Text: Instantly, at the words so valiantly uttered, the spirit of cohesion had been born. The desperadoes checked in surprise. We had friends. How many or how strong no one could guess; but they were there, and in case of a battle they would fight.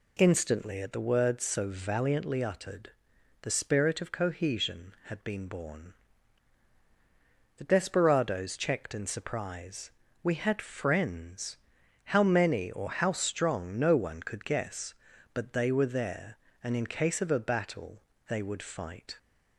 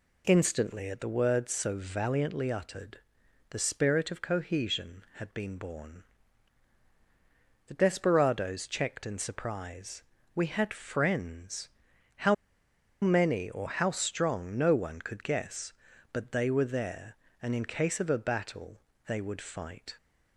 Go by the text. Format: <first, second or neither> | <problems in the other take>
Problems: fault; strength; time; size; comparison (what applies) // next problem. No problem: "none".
first | pauses between "How" and "many"; noticeable; at 12.3 s; 0.68 s long // pauses between "battle" and "they"; slight; at 18.7 s; 0.28 s long; slight in the first